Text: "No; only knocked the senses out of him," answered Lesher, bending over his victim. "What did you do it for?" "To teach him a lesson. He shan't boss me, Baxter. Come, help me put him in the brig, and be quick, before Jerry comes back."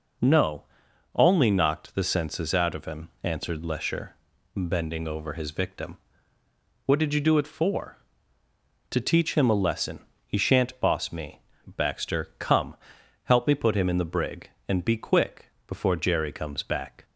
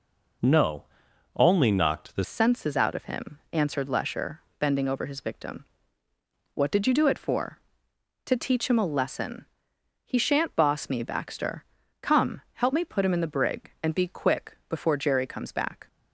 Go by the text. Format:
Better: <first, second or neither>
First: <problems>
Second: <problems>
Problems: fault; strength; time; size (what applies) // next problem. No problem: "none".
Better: first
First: none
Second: changes voice at "senses"; from 2.2 s on; 13.6 s long